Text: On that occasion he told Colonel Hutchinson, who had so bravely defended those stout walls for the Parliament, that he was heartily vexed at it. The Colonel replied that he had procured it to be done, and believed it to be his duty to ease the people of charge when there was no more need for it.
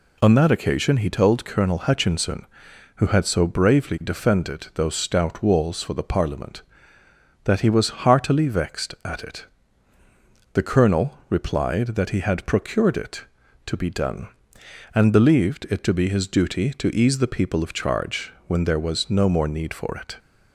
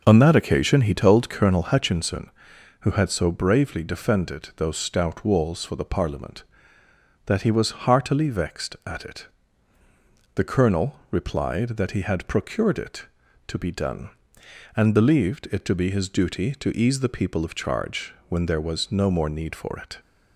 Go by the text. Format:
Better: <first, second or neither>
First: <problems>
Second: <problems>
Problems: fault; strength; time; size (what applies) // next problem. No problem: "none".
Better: first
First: pauses between "charge" and "when"; slight; at 18.3 s; 0.16 s long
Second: starts louder than the rest; noticeable; until 1.9 s; 5.5 dB // pauses between "charge" and "when"; slight; at 18.1 s; 0.16 s long